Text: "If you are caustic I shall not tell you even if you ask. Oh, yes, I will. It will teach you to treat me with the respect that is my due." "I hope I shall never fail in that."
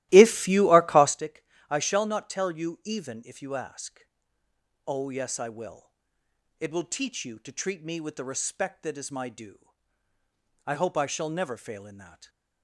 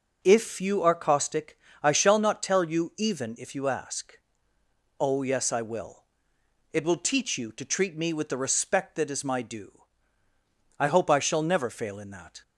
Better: second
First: starts louder than the rest; strong; until 1.2 s; 16 dB // pauses between "caustic" and "I"; slight; at 1.4 s; 0.24 s long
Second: pauses between "caustic" and "I"; slight; at 1.5 s; 0.24 s long

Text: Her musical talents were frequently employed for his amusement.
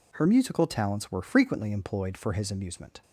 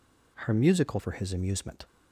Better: first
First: none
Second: skips "talents were frequently employed"; at 0.9 s

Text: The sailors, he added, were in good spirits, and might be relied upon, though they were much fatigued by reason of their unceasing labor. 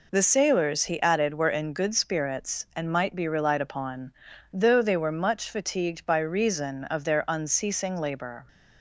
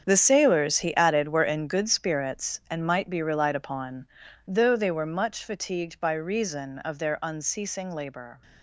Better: first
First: none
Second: gets quieter; strong; throughout; 13 dB

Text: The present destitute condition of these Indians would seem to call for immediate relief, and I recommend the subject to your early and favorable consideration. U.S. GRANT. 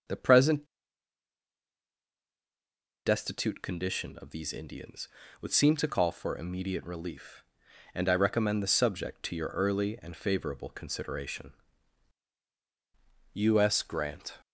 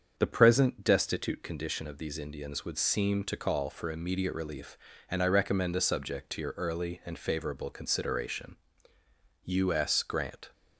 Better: second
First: starts louder than the rest; until 3.5 s; 6.5 dB // pauses between "present" and "destitute"; strong; at 0.6 s; 2.4 s long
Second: starts louder than the rest; strong; until 1.1 s; 7 dB

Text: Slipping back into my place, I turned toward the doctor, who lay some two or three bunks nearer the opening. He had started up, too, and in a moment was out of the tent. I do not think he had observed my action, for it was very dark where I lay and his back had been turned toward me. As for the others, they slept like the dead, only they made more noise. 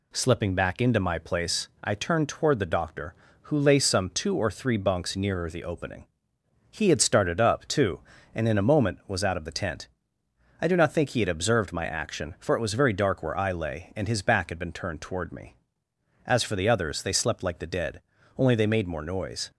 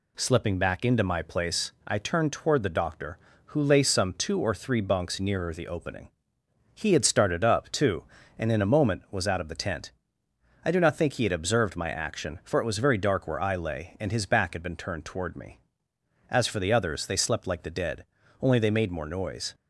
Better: neither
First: none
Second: none

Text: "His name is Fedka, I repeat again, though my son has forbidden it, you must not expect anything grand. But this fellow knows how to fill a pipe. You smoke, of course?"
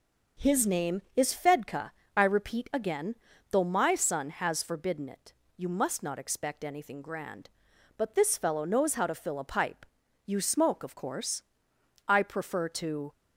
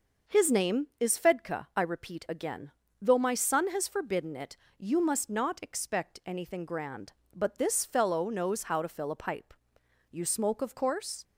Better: second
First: starts louder than the rest; noticeable; until 1.5 s; 6 dB // goes on to say "I prefer to"; noticeable; from 12.0 s on; 1.0 s long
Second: none

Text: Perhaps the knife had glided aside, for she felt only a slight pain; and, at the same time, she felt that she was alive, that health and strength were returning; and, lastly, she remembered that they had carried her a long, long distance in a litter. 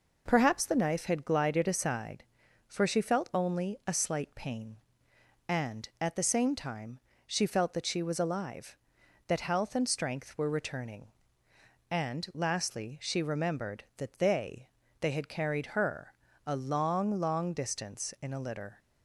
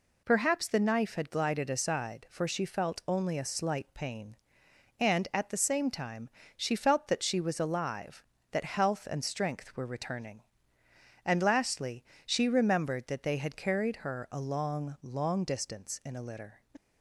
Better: second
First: says "they" twice; at 14.9 s // pauses between "her" and "a"; slight; at 16.1 s; 0.32 s long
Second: none

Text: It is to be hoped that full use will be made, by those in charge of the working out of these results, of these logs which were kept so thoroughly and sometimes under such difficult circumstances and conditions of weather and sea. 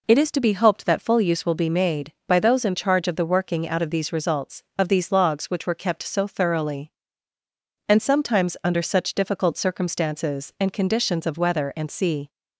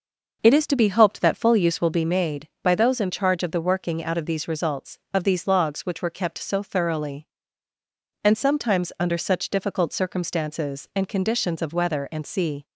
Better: first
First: none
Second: starts louder than the rest; noticeable; until 2.1 s; 6 dB

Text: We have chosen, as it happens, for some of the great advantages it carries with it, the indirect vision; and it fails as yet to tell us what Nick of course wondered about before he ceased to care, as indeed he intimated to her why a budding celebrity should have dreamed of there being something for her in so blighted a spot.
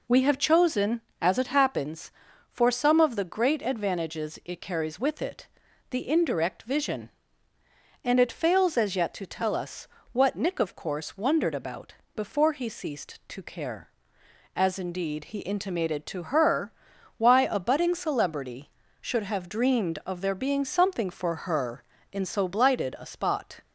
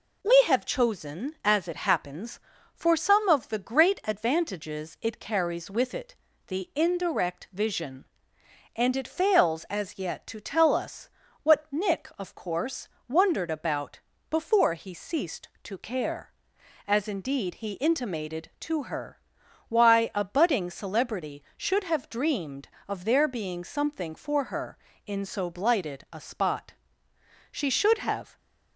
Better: first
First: pauses between "us" and "what"; slight; at 9.8 s; 0.24 s long // pauses between "about" and "before"; slight; at 11.9 s; 0.20 s long // pauses between "her" and "why"; noticeable; at 16.7 s; 0.46 s long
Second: pauses between "us" and "what"; slight; at 11.0 s; 0.36 s long // pauses between "course" and "wondered"; slight; at 12.8 s; 0.20 s long // pauses between "about" and "before"; slight; at 13.9 s; 0.32 s long // pauses between "her" and "why"; noticeable; at 19.1 s; 0.48 s long // goes on to say "She should have"; noticeable; from 27.5 s on; 0.86 s long

